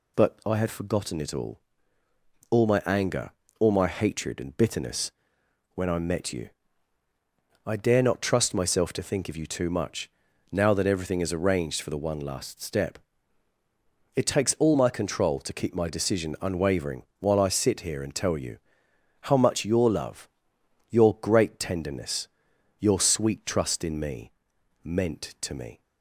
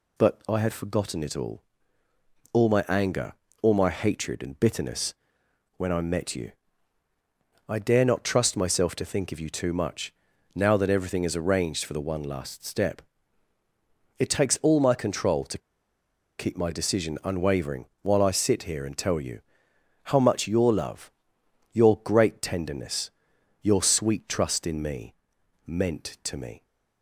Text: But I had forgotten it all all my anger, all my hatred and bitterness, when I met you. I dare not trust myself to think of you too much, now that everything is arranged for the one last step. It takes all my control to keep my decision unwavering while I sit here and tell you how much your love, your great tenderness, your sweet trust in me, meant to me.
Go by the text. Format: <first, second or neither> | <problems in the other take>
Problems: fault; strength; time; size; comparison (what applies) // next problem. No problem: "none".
first | pauses between "all" and "all"; noticeable; at 1.6 s; 0.90 s long; noticeable in the first // pauses between "to" and "keep"; noticeable; at 15.5 s; 0.79 s long // pauses between "unwavering" and "while"; slight; at 17.8 s; 0.16 s long; slight in the first // pauses between "you" and "how"; noticeable; at 19.4 s; 0.64 s long; noticeable in the first